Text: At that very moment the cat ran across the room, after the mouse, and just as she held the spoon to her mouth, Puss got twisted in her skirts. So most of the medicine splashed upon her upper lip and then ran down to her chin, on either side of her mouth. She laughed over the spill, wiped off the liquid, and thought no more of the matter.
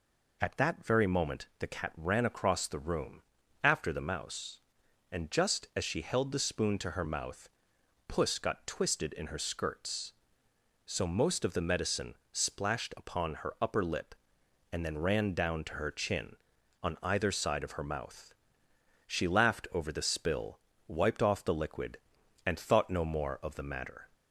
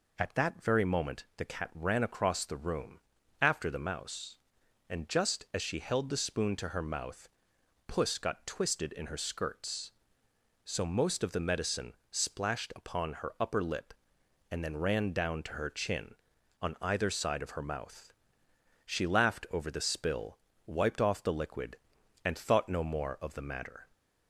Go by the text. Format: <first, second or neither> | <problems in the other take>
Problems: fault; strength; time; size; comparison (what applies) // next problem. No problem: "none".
neither | pauses between "medicine" and "splashed"; slight; the same in both